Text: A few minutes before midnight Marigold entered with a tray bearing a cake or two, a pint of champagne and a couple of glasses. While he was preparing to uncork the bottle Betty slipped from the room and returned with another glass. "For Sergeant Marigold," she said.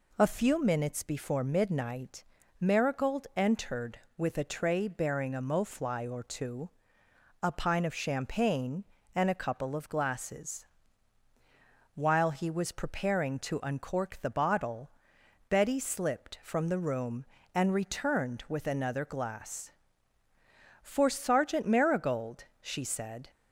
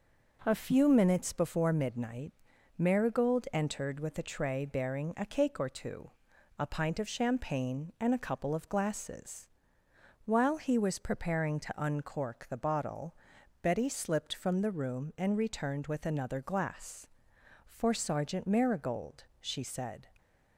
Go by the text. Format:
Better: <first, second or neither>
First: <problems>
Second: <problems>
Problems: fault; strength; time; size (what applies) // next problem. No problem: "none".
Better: second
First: pauses between "midnight" and "Marigold"; slight; at 2.2 s; 0.36 s long // says "mofly" for "cake"; at 5.3 s // pauses between "bottle" and "Betty"; noticeable; at 14.8 s; 0.58 s long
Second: pauses between "midnight" and "Marigold"; noticeable; at 2.3 s; 0.46 s long // pauses between "bottle" and "Betty"; noticeable; at 13.1 s; 0.46 s long